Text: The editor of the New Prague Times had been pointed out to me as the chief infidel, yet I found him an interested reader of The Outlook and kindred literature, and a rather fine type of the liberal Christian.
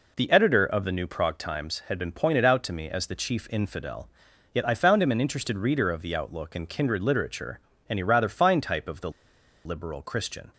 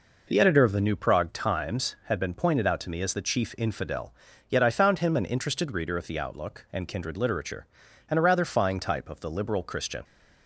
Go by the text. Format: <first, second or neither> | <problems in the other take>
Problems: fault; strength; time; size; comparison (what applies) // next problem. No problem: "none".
second | pauses between "the" and "liberal"; noticeable; at 9.0 s; 0.55 s long